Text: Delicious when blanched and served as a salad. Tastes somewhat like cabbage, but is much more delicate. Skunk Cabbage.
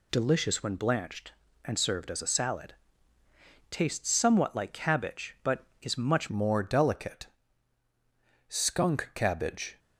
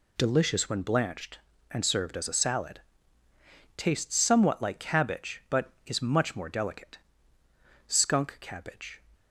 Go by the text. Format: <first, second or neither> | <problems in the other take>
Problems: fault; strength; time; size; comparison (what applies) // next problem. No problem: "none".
second | changes voice at "more"; from 6.2 s on; 3.5 s long